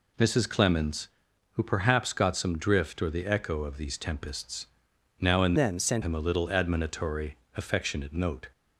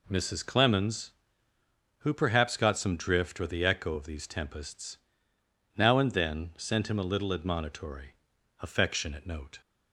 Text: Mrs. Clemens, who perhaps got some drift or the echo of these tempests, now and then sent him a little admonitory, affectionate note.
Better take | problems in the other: second | changes voice from "then" to "sent"; from 5.5 to 6.0 s; 0.5 s long

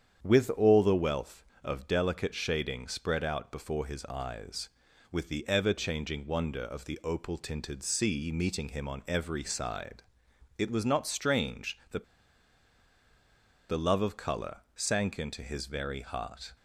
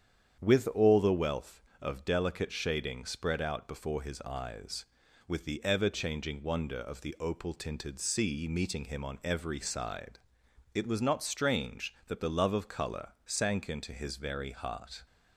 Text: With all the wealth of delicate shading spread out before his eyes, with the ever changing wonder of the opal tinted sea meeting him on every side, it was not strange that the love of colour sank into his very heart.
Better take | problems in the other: second | starts louder than the rest; strong; until 1.2 s; 8.5 dB; strong in the second // pauses between "that" and "the"; strong; at 12.0 s; 1.6 s long

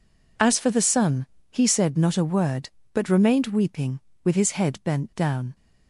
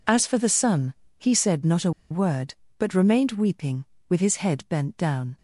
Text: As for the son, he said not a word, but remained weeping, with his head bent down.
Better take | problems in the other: first | pauses between "a" and "word"; slight; at 1.9 s; 0.19 s long

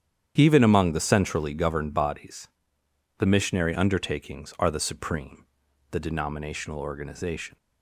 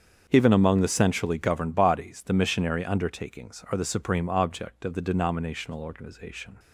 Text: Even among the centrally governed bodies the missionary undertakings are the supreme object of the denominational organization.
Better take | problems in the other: second | starts louder than the rest; strong; until 1.3 s; 9 dB; strong in the second // pauses between "bodies" and "the"; noticeable; at 2.4 s; 0.70 s long // skips "object of"; at 5.6 s

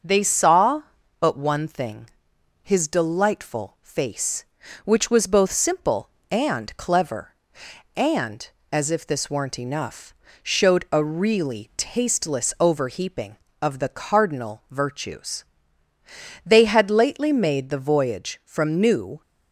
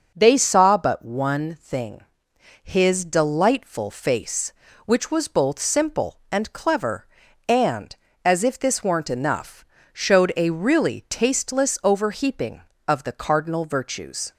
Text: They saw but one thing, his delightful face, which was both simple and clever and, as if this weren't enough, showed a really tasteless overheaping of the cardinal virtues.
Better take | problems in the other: second | goes on to say "They had lately made the voyage from New"; strong; from 16.4 s on; 2.7 s long

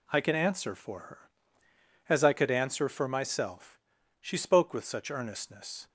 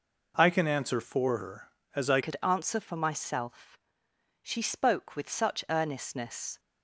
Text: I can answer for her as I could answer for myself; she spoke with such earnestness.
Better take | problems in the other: first | changes voice at "could"; from 2.2 s on; 4.3 s long

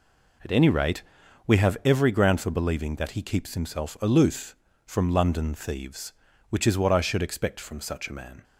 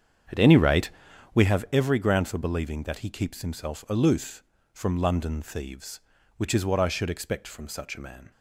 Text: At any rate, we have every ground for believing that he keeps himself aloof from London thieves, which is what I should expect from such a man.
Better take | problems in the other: first | starts louder than the rest; strong; until 1.5 s; 8 dB

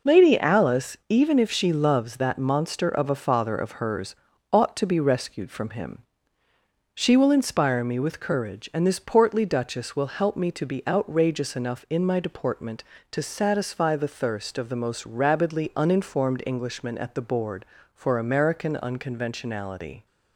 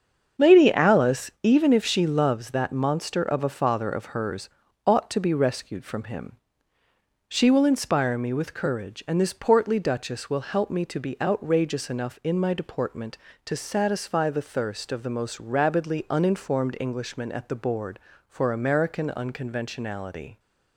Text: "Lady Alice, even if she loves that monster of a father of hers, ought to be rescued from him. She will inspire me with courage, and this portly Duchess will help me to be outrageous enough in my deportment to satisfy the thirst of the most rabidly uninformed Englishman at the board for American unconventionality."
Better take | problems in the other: first | starts louder than the rest; strong; until 2.1 s; 7 dB

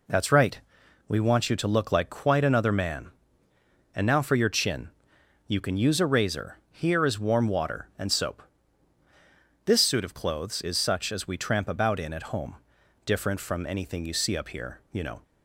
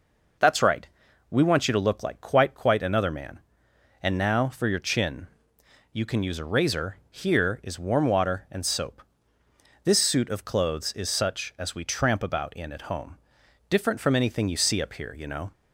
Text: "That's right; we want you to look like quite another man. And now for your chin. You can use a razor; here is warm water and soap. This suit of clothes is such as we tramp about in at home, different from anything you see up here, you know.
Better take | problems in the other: first | says "quite" twice; at 2.5 s

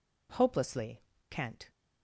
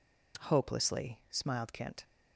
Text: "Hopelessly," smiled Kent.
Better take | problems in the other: second | skips "smiled"; at 1.1 s

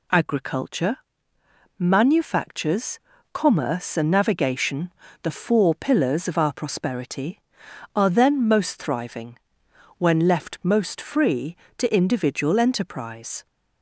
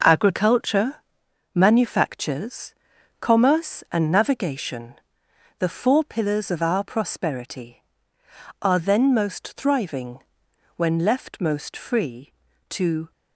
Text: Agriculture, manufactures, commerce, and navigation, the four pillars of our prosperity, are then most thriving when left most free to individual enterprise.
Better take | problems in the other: first | pauses between "thriving" and "when"; noticeable; at 10.1 s; 0.58 s long; noticeable in the first // stops before "individual enterprise"; at 13.1 s

